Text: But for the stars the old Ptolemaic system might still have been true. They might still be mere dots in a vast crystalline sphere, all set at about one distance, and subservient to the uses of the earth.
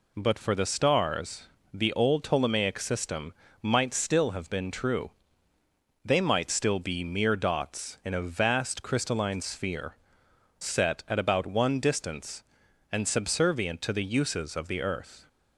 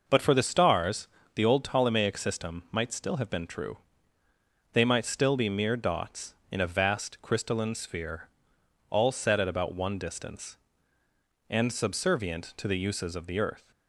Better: second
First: pauses between "stars" and "the"; slight; at 1.4 s; 0.26 s long // pauses between "system" and "might"; slight; at 3.3 s; 0.30 s long // skips "all"; at 10.2 s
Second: pauses between "stars" and "the"; slight; at 1.0 s; 0.28 s long

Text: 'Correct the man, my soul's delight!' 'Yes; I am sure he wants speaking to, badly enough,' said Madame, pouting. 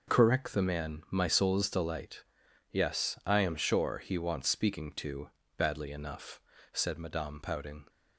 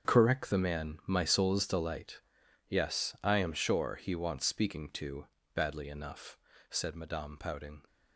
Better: first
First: none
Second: gets quieter; strong; throughout; 12.5 dB

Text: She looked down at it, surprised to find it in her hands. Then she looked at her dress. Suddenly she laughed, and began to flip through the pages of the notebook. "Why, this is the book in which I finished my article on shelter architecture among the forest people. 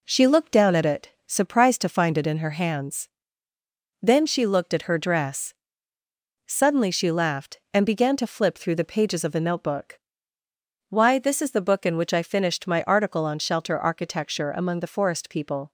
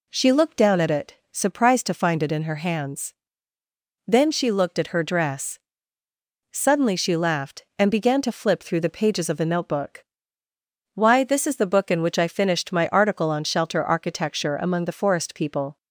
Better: second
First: gets quieter; noticeable; throughout; 4 dB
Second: none

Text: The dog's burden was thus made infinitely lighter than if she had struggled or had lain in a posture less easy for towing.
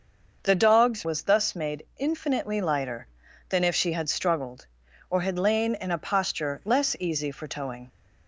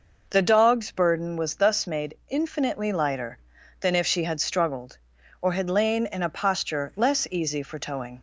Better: second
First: starts louder than the rest; noticeable; until 1.4 s; 6 dB // skips "burden"; at 1.0 s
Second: none

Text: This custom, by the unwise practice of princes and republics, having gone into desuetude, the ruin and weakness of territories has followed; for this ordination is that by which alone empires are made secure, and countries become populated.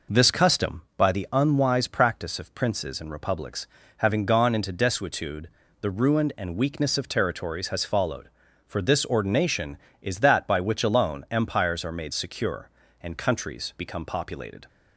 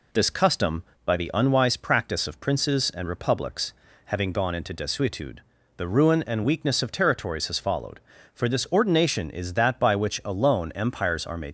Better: first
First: none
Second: stops before "secure and countries become populated"; at 11.4 s

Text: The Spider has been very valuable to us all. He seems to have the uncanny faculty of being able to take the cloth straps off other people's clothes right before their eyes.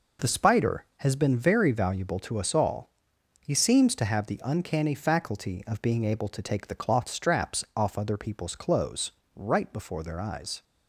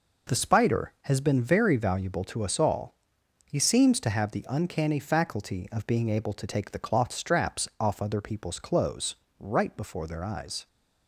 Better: neither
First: pauses between "clothes" and "right"; slight; at 9.1 s; 0.24 s long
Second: pauses between "clothes" and "right"; slight; at 9.1 s; 0.24 s long

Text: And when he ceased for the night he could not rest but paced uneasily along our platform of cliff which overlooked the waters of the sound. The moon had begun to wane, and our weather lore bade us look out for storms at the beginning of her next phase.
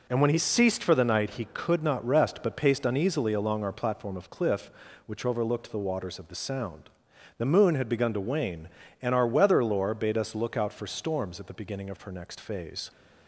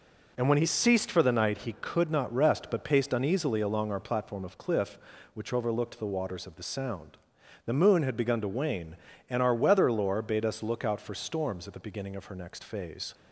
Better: neither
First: none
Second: none

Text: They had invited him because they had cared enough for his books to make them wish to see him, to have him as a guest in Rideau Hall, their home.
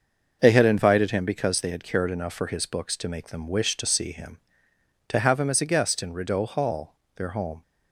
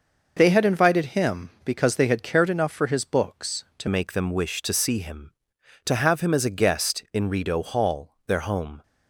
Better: first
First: none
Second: changes voice at "make"; from 3.8 s on; 5.0 s long

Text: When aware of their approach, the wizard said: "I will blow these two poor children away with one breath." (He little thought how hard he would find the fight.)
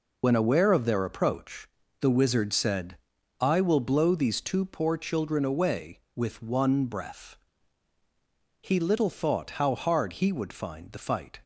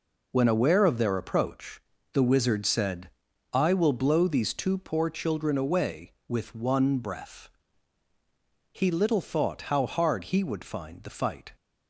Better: second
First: loses the start of "When"; at 0.2 s; 30 ms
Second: none

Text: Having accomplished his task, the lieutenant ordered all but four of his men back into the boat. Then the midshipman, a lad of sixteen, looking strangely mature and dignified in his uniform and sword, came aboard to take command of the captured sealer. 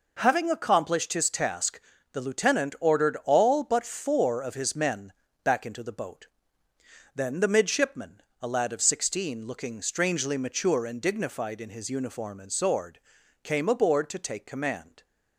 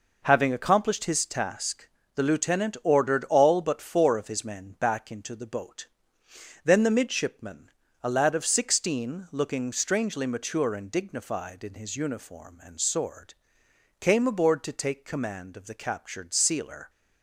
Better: second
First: pauses between "men" and "back"; slight; at 5.1 s; 0.32 s long // stops before "of the captured sealer"; at 15.0 s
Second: none

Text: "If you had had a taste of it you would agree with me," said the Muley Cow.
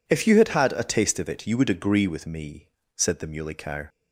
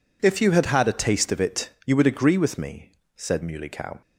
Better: first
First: none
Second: pauses between "it" and "you"; slight; at 1.6 s; 0.16 s long // skips "the"; at 3.4 s

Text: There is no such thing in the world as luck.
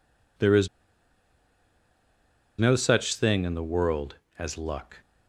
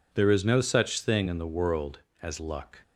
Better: second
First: pauses between "is" and "no"; strong; at 0.6 s; 1.9 s long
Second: none

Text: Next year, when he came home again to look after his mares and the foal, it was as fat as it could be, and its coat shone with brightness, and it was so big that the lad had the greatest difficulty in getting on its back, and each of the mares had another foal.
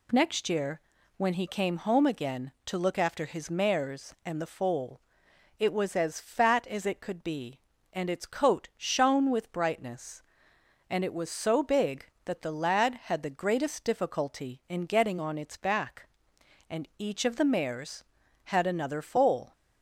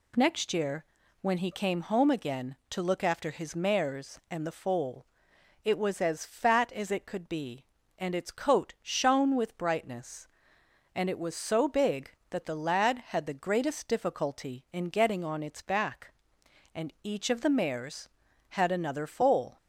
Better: neither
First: none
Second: none

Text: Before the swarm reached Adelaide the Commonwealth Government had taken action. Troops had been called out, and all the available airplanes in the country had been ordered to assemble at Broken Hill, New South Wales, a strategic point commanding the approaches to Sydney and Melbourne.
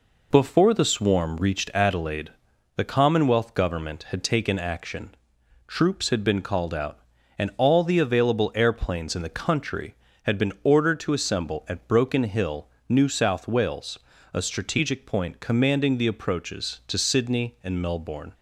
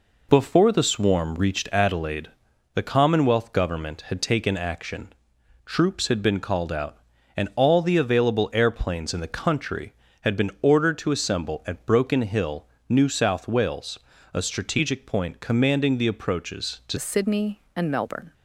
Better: first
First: pauses between "Adelaide" and "the"; noticeable; at 2.2 s; 0.48 s long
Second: pauses between "Adelaide" and "the"; noticeable; at 2.2 s; 0.48 s long // changes voice at "Sydney"; from 16.9 s on; 1.4 s long

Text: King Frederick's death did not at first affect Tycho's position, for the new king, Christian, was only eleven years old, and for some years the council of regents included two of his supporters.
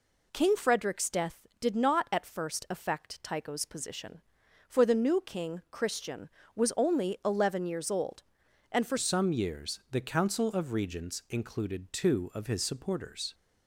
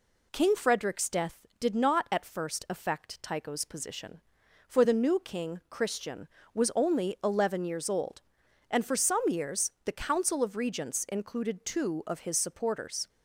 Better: second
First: changes voice at "some"; from 8.9 s on; 4.4 s long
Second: none

